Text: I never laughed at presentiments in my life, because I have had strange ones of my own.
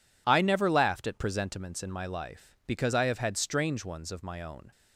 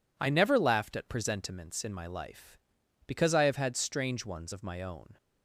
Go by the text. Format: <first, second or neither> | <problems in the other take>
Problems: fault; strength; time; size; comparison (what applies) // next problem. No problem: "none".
neither | none